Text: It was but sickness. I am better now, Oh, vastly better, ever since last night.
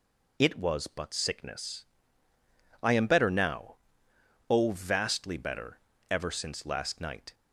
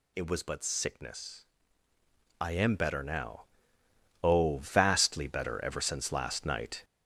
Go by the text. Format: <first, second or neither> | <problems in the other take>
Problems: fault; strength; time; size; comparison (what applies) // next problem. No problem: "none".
first | gets louder; noticeable; throughout; 5.5 dB